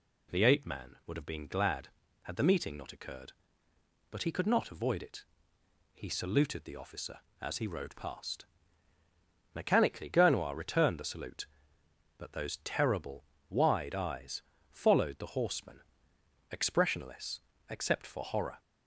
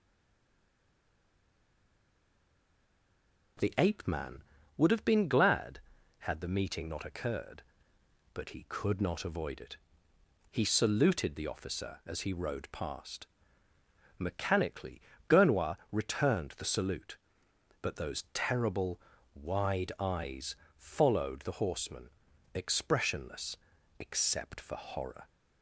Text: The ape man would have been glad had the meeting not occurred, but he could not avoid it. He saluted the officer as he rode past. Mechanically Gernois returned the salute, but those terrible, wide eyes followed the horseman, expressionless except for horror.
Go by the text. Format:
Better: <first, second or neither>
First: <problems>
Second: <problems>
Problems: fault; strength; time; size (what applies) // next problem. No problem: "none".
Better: first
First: pauses between "eyes" and "followed"; slight; at 14.4 s; 0.26 s long // pauses between "expressionless" and "except"; slight; at 17.3 s; 0.28 s long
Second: stays silent before the first word; strong; until 3.5 s; 3.5 s long // pauses between "Mechanically" and "Gernois"; slight; at 15.0 s; 0.28 s long // pauses between "Gernois" and "returned"; slight; at 15.7 s; 0.16 s long // pauses between "eyes" and "followed"; slight; at 20.5 s; 0.22 s long // pauses between "expressionless" and "except"; at 23.5 s; 0.42 s long